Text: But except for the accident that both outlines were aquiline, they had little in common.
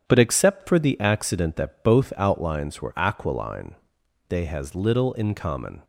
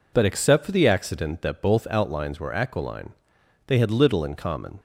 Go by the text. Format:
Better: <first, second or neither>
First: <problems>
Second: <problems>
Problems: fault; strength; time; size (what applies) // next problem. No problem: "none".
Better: second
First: starts louder than the rest; strong; until 1.0 s; 9 dB // says "has" for "had"; at 4.4 s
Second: none